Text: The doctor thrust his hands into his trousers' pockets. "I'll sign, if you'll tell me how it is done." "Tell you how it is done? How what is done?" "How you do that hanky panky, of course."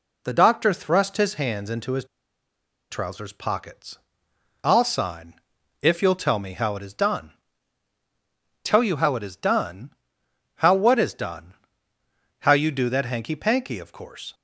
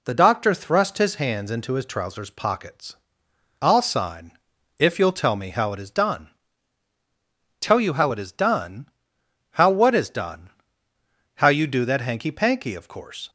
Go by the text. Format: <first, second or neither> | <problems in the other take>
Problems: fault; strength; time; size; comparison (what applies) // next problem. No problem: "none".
second | pauses between "his" and "trousers"; noticeable; at 2.0 s; 0.86 s long